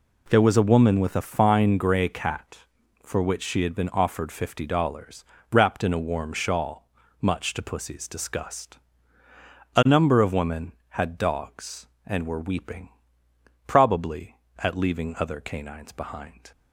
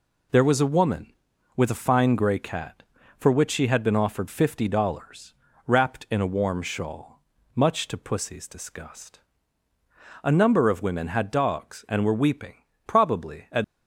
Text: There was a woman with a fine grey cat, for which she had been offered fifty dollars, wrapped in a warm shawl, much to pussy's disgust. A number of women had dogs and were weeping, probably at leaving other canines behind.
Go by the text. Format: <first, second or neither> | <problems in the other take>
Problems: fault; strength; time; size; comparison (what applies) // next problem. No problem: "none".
first | stops before "leaving other canines behind"; at 13.6 s